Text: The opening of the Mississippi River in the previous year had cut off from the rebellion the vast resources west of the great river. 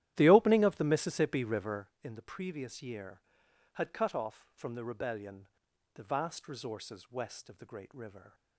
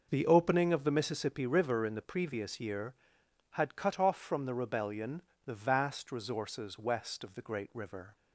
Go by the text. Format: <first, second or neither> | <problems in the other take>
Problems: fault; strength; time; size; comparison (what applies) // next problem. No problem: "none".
second | starts louder than the rest; strong; until 1.9 s; 12.5 dB // pauses between "rebellion" and "the"; noticeable; at 5.4 s; 0.48 s long; slight in the second